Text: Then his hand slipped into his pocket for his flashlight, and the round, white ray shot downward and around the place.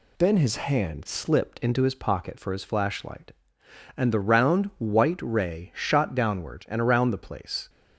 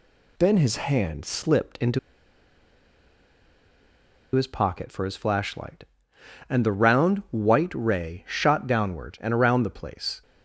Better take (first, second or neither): first